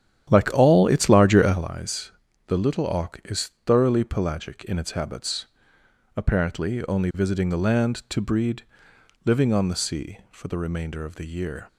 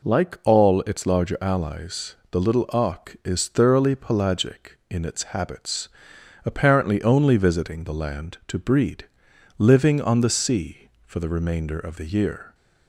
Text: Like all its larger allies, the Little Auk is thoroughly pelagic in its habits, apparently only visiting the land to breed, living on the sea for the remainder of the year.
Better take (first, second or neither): second